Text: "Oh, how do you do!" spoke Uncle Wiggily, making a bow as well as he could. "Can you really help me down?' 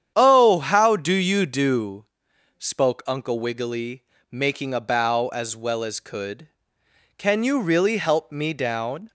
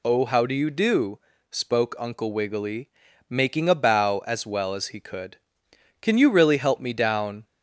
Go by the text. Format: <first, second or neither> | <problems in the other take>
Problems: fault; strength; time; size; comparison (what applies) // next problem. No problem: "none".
second | starts louder than the rest; strong; until 1.1 s; 9 dB // skips "he"; at 6.0 s